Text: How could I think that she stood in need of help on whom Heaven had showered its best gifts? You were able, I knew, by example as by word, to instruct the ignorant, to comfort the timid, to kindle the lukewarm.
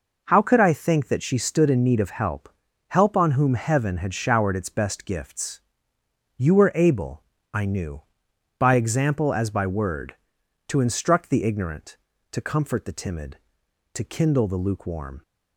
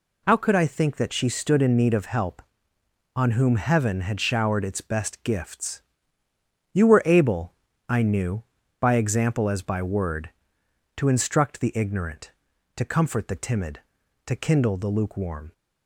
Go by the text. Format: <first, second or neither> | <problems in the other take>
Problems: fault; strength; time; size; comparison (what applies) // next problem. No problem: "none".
second | says "help" twice; at 2.8 s